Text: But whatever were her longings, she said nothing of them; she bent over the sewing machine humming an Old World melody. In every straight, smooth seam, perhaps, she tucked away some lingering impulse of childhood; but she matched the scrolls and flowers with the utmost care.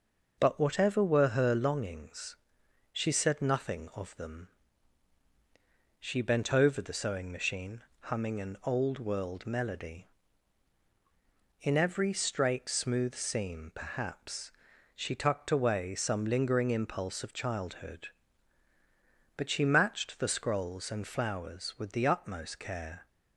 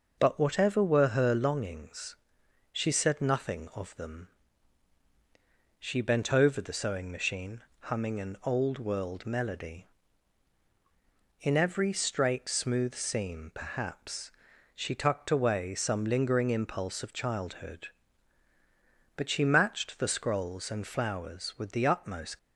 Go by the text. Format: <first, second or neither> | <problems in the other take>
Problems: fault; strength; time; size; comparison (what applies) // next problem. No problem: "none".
first | pauses between "machine" and "humming"; slight; at 7.6 s; 0.20 s long; slight in the first // stops before "care"; at 22.3 s